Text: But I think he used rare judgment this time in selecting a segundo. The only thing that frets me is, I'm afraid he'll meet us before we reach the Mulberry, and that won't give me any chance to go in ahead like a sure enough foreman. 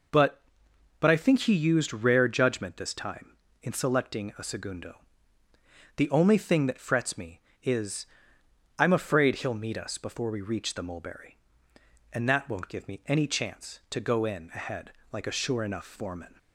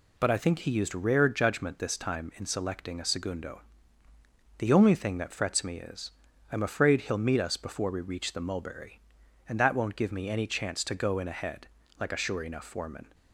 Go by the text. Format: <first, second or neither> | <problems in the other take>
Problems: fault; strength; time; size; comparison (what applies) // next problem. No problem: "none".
second | says "But" twice; at 0.9 s // pauses between "ahead" and "like"; slight; at 14.9 s; 0.22 s long; slight in the second